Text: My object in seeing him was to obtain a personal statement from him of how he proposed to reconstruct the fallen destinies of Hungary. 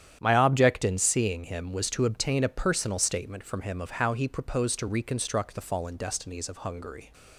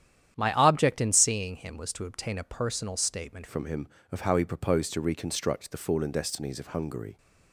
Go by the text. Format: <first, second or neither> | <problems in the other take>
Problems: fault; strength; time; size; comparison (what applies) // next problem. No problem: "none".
first | starts louder than the rest; strong; until 1.3 s; 10 dB; strong in the first // changes voice at "from"; from 3.4 s on; 3.7 s long